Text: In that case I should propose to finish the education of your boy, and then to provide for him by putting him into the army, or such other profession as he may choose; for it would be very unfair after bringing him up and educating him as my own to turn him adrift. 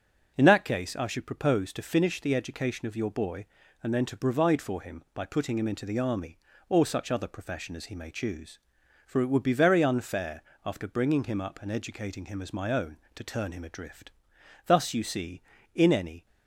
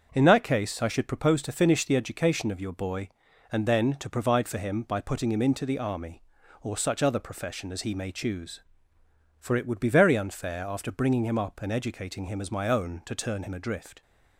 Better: second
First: starts louder than the rest; strong; until 1.3 s; 7.5 dB // pauses between "unfair" and "after"; slight; at 10.4 s; 0.22 s long // goes on to say "Thus you see in any"; from 14.6 s on; 1.5 s long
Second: starts louder than the rest; until 1.1 s; 7 dB

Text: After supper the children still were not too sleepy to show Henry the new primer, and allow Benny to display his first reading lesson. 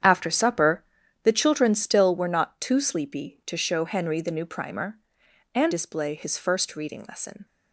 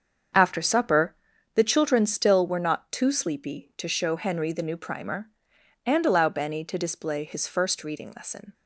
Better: second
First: starts louder than the rest; strong; until 1.4 s; 8.5 dB // pauses between "supper" and "the"; at 0.8 s; 0.40 s long // skips "allow Benny to"; at 5.7 s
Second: starts louder than the rest; until 1.7 s; 7 dB // pauses between "supper" and "the"; at 1.1 s; 0.40 s long

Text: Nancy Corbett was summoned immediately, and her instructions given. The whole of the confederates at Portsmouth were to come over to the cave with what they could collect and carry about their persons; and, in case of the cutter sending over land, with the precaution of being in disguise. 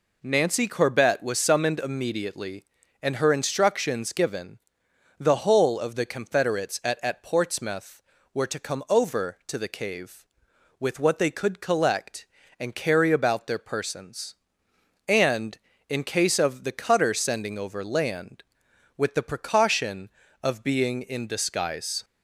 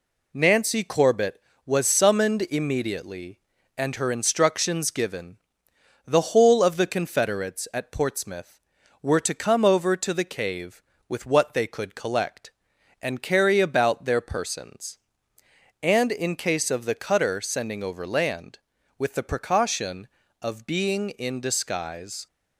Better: second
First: says "at" twice; at 7.0 s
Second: none

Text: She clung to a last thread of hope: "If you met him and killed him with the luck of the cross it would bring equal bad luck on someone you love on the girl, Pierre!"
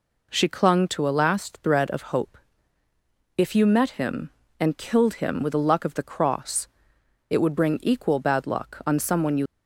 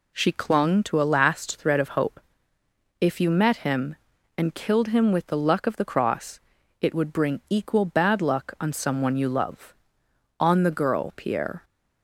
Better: second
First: pauses between "cross" and "it"; noticeable; at 6.6 s; 0.64 s long // stops before "love on the girl Pierre"; at 9.4 s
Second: pauses between "cross" and "it"; at 6.3 s; 0.42 s long

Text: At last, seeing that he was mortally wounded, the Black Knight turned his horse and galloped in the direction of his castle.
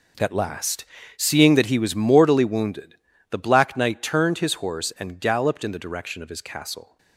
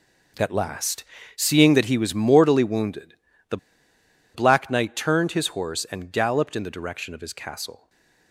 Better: first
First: none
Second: pauses between "the" and "Black"; noticeable; at 3.5 s; 0.77 s long // stays silent after the last word; slight; from 7.7 s on; 0.6 s long

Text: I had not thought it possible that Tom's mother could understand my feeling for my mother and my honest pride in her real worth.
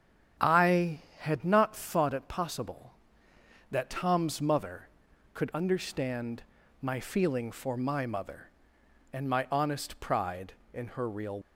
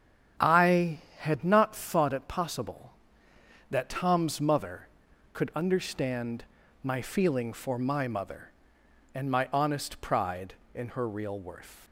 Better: second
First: starts louder than the rest; strong; until 1.6 s; 8.5 dB // pauses between "understand" and "my"; at 6.4 s; 0.38 s long // stops before "worth"; at 11.4 s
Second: starts louder than the rest; strong; until 1.5 s; 8.5 dB // pauses between "understand" and "my"; at 6.4 s; 0.38 s long

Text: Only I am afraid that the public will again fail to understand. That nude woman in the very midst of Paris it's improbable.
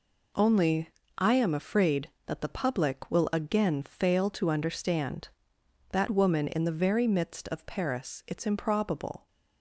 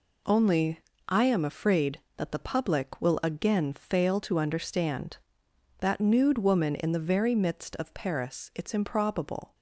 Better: second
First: pauses between "Only" and "I"; slight; at 0.8 s; 0.28 s long // skips "nude"; at 6.0 s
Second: pauses between "Only" and "I"; slight; at 0.8 s; 0.28 s long

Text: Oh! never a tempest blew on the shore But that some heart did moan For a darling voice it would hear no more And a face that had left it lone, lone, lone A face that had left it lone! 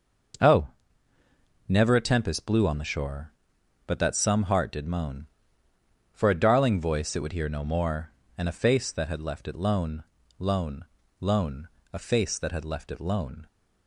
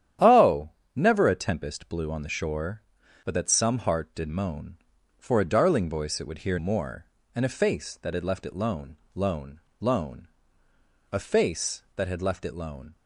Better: first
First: starts louder than the rest; noticeable; until 2.4 s; 6 dB // pauses between "lone" and "A"; slight; at 11.6 s; 0.24 s long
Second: starts louder than the rest; strong; until 1.4 s; 10 dB // skips "no"; at 6.5 s // pauses between "lone" and "A"; noticeable; at 10.2 s; 0.86 s long

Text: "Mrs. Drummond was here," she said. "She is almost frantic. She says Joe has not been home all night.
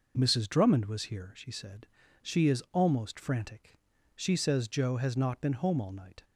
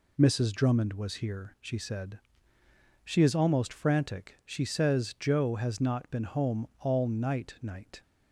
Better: first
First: none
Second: says "night" twice; at 7.6 s

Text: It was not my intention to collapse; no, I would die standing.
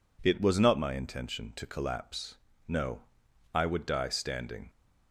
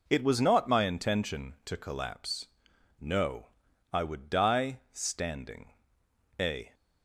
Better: first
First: none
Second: goes on to say "A"; slight; from 6.3 s on; 0.34 s long

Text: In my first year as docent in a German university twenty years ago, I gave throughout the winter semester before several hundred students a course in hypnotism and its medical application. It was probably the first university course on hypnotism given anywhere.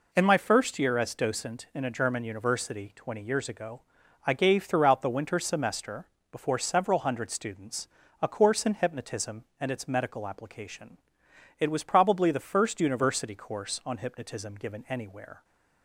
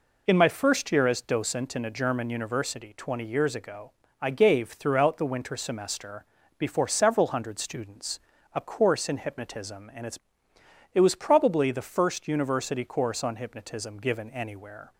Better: first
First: pauses between "semester" and "before"; slight; at 6.0 s; 0.26 s long // pauses between "students" and "a"; slight; at 7.8 s; 0.32 s long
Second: pauses between "semester" and "before"; slight; at 6.2 s; 0.34 s long // pauses between "students" and "a"; slight; at 8.1 s; 0.34 s long // skips "medical application"; at 10.5 s

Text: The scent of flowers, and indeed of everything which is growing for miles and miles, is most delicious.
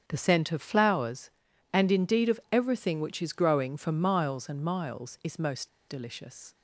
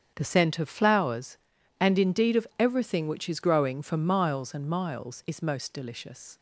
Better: second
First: starts louder than the rest; strong; until 1.0 s; 8 dB // pauses between "most" and "delicious"; slight; at 5.6 s; 0.20 s long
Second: starts louder than the rest; strong; until 1.1 s; 8 dB

